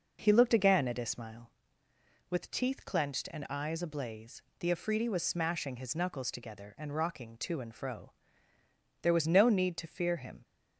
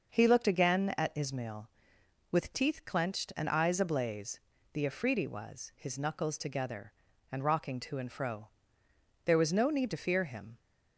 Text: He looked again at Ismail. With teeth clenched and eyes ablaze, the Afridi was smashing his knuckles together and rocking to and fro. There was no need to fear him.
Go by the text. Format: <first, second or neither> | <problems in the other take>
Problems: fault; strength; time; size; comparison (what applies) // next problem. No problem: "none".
first | starts louder than the rest; noticeable; until 1.1 s; 6 dB // skips "smashing"; at 5.7 s